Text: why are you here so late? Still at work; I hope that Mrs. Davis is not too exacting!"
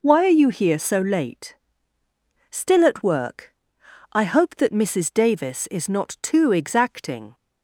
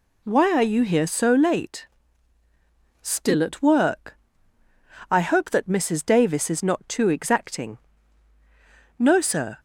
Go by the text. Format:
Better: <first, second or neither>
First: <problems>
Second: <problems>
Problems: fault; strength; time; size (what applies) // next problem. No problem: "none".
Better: first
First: none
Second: goes on to say "No sir"; from 8.9 s on; 0.58 s long